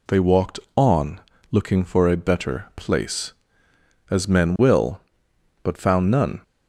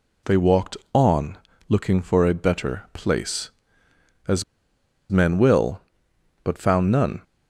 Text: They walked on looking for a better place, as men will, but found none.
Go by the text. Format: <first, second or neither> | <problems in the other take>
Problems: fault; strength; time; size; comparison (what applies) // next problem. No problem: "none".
first | pauses between "on" and "looking"; slight; at 1.3 s; 0.32 s long; slight in the first // pauses between "as" and "men"; noticeable; at 4.4 s; 0.68 s long